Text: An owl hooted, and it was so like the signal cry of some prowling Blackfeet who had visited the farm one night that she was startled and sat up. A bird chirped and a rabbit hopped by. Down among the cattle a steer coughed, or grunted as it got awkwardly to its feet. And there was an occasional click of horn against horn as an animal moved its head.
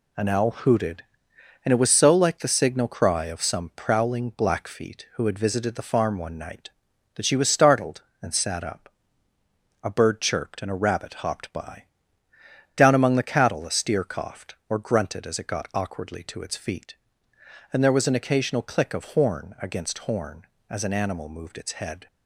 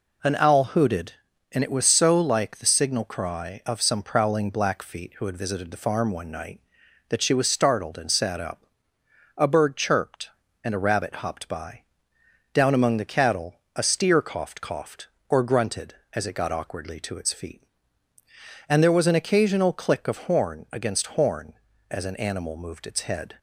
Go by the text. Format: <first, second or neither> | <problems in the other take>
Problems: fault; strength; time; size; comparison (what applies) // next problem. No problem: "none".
first | pauses between "cattle" and "a"; slight; at 13.6 s; 0.16 s long // says "coughed" twice; at 14.6 s